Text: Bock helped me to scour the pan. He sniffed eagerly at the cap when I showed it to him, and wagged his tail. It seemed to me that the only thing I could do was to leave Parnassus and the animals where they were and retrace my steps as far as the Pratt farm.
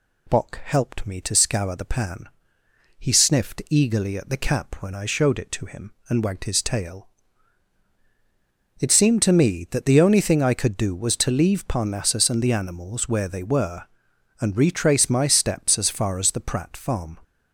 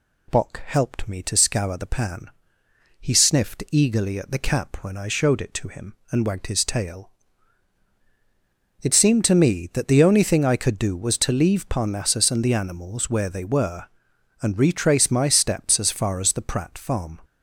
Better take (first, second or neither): neither